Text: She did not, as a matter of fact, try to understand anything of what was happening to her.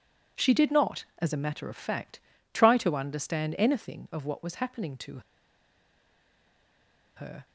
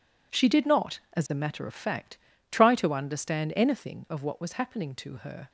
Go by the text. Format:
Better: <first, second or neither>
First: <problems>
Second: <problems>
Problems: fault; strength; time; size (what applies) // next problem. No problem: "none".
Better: second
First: pauses between "to" and "her"; strong; at 5.1 s; 1.9 s long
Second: none